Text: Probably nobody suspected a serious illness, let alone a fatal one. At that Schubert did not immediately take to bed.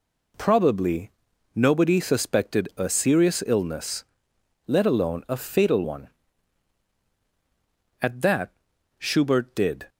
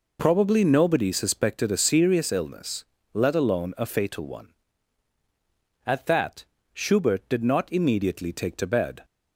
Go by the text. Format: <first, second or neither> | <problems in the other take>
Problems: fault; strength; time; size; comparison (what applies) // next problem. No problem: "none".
second | pauses between "Probably" and "nobody"; at 1.1 s; 0.44 s long // pauses between "that" and "Schubert"; noticeable; at 8.4 s; 0.48 s long; slight in the second // stops before "not immediately take to bed"; at 9.8 s